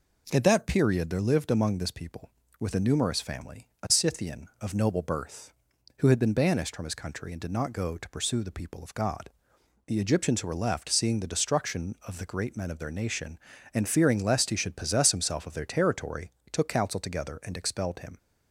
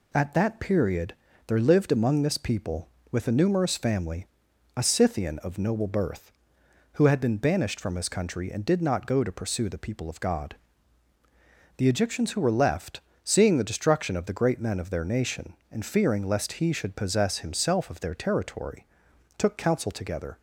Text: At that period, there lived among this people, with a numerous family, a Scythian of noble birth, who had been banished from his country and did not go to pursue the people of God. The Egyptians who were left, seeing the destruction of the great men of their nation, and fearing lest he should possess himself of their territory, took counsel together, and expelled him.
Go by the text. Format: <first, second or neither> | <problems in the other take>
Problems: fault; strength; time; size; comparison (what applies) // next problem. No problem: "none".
first | stops before "and expelled him"; at 20.3 s